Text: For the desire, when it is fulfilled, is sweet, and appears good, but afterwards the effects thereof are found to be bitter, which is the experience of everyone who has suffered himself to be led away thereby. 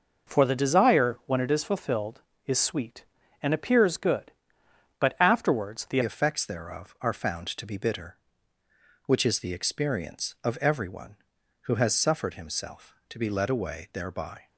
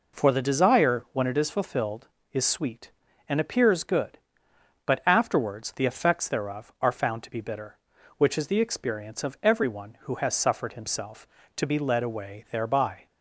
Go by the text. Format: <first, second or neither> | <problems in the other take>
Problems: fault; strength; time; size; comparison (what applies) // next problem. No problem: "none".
second | changes voice at "effects"; from 6.0 s on; 8.4 s long